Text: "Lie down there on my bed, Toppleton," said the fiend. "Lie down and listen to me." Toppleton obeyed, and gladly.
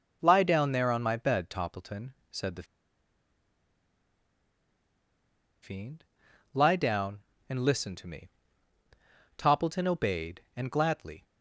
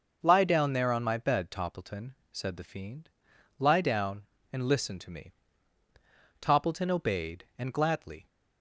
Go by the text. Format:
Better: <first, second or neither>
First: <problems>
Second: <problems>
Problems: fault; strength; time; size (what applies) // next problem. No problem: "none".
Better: second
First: pauses between "the" and "fiend"; strong; at 2.6 s; 2.9 s long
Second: none